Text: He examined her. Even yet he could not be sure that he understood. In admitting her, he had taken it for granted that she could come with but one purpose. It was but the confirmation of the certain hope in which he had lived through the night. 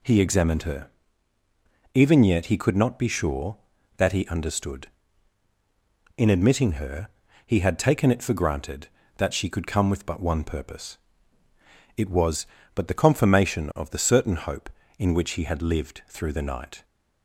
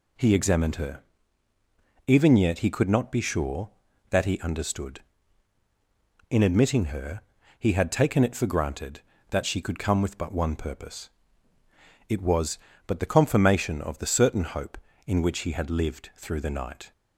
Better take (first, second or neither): neither